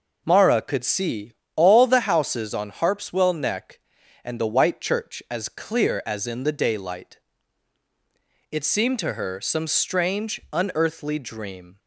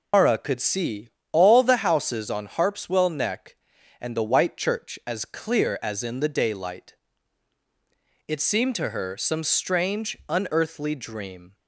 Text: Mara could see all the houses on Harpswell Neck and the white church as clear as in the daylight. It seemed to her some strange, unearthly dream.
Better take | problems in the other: first | loses the start of "Mara"; at 0.1 s; 130 ms // pauses between "see" and "all"; slight; at 1.0 s; 0.24 s long; slight in the first

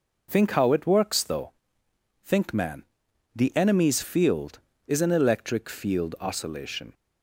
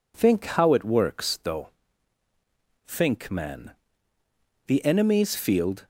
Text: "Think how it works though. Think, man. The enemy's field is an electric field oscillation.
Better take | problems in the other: first | stops before "is an electric field oscillation"; at 5.8 s

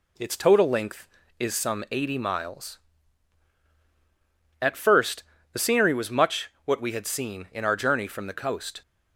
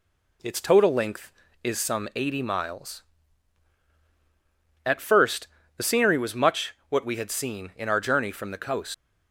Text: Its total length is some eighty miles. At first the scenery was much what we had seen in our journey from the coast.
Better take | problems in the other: first | pauses between "first" and "the"; slight; at 5.4 s; 0.28 s long; slight in the first // leaves "coast" unfinished; at 8.9 s; 110 ms

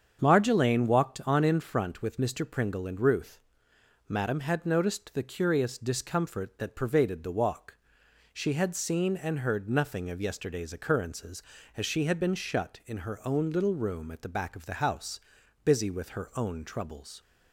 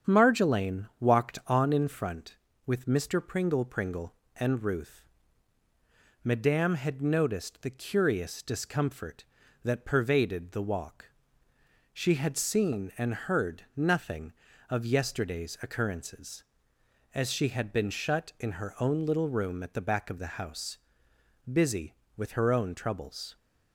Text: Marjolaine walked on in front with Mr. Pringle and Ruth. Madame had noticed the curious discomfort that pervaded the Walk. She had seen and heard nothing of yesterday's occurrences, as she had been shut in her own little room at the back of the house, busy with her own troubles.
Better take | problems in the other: first | starts louder than the rest; strong; until 1.2 s; 8 dB; strong in the first // says "Pringle" twice; at 3.6 s

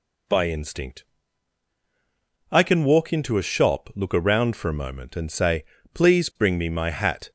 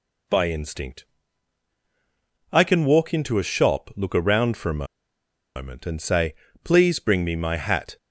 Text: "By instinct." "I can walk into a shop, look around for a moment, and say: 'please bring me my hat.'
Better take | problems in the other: first | pauses between "a" and "moment"; noticeable; at 4.8 s; 0.72 s long

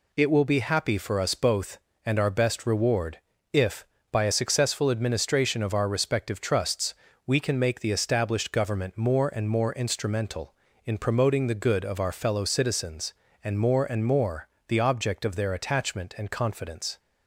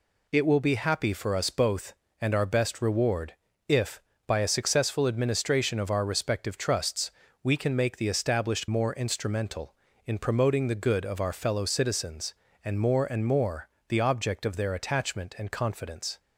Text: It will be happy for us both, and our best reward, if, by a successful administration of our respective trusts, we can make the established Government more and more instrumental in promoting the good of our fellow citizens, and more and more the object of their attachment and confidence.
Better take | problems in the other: first | skips "Government more and"; at 8.6 s // pauses between "more" and "the"; slight; at 13.6 s; 0.18 s long; slight in the first

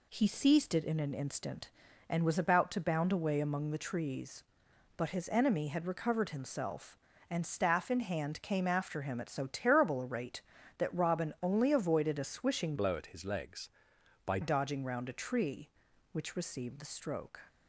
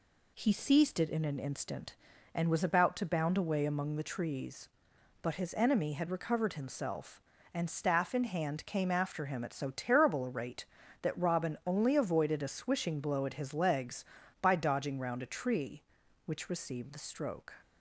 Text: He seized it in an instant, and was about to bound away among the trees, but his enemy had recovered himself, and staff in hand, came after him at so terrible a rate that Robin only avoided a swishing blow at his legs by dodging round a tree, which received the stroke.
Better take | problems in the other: second | changes voice from "blow" to "by"; from 12.7 to 14.3 s; 1.6 s long

